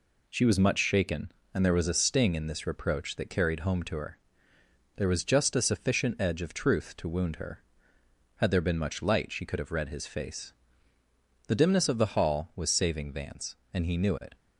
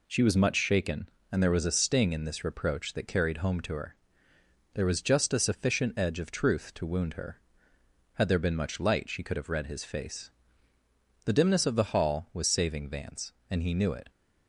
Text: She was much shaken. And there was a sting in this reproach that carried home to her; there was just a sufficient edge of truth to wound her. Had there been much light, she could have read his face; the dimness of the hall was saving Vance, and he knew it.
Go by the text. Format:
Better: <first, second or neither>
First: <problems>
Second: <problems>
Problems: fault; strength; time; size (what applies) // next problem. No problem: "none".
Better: neither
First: none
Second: none